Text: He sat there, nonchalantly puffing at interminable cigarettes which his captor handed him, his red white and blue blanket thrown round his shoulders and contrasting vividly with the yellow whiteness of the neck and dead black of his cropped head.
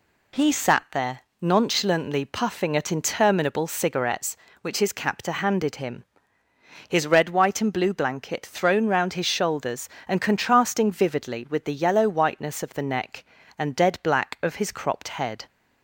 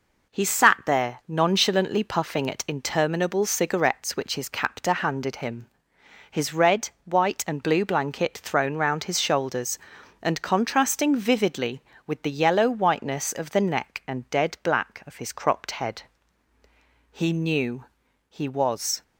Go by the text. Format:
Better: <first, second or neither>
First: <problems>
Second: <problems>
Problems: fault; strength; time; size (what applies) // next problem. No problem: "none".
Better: first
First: none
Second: pauses between "red" and "white"; slight; at 6.9 s; 0.16 s long // goes on to say "He knew he was"; strong; from 17.1 s on; 1.8 s long